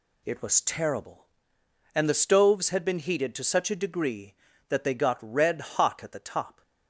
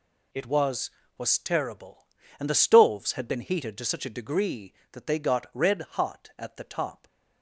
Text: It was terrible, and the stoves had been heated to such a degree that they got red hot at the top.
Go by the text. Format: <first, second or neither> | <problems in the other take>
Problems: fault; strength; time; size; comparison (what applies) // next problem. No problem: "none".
first | says "was" twice; at 1.1 s